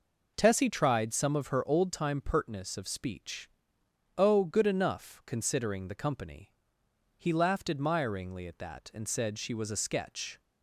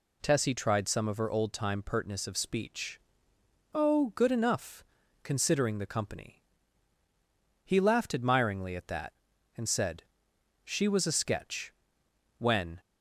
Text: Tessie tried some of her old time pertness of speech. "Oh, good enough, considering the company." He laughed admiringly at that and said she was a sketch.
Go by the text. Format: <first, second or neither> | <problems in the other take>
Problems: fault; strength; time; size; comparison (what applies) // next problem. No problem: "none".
first | pauses between "said" and "she"; noticeable; at 10.0 s; 0.60 s long // goes on to say "When"; slight; from 12.3 s on; 0.42 s long